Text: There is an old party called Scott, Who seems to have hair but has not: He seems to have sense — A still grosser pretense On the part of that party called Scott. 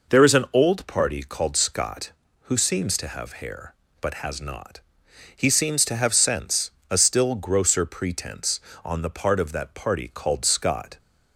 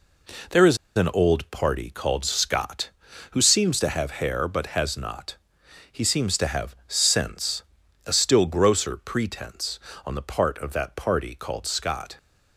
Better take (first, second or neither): first